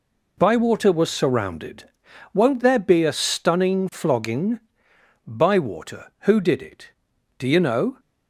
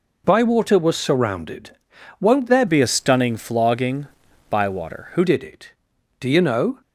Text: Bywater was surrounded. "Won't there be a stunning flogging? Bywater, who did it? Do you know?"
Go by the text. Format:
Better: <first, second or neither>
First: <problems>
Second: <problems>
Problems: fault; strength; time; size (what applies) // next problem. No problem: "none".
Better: first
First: none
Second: changes voice from "be" to "who"; from 2.6 to 5.2 s; 2.6 s long